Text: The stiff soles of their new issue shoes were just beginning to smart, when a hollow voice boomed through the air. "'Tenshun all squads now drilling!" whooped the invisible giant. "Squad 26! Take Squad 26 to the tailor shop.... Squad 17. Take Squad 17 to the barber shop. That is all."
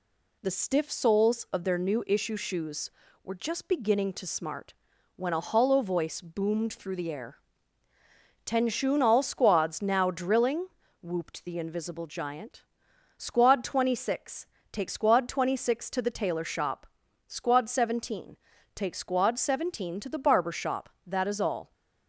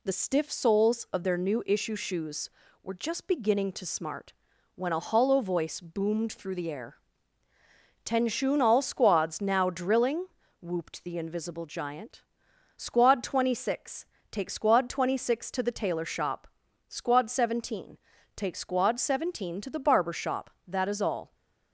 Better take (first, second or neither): neither